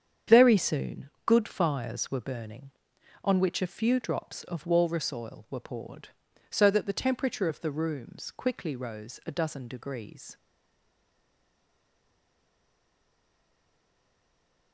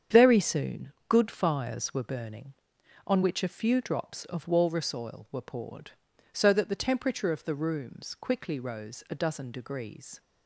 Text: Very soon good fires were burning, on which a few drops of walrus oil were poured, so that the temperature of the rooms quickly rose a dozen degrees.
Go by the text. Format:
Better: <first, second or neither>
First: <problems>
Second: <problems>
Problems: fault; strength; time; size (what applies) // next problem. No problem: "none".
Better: second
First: starts louder than the rest; strong; until 1.4 s; 8 dB // pauses between "soon" and "good"; slight; at 1.0 s; 0.16 s long // stays silent after the last word; strong; from 10.3 s on; 4.4 s long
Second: starts louder than the rest; strong; until 1.2 s; 8 dB // pauses between "soon" and "good"; slight; at 0.9 s; 0.16 s long